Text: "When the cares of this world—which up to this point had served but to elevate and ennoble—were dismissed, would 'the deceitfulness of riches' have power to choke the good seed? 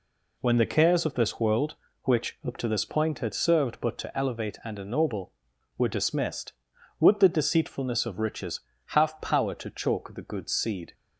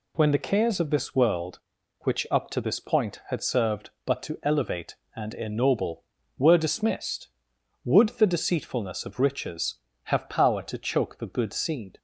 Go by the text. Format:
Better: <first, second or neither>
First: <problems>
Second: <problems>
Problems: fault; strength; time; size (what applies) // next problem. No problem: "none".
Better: neither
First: none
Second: none